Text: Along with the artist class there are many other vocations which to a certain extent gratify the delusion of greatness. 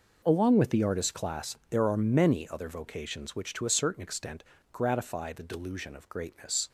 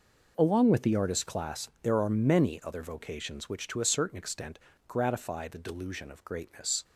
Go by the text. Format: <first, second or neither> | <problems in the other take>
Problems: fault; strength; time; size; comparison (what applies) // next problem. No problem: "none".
neither | pauses between "extent" and "gratify"; slight; the same in both